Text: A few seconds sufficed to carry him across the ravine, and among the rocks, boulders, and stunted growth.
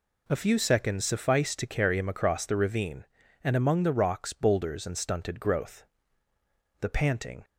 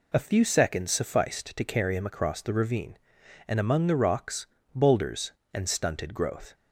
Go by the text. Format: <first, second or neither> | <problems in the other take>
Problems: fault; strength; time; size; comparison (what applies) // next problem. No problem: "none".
second | goes on to say "The panting"; noticeable; from 6.8 s on; 0.64 s long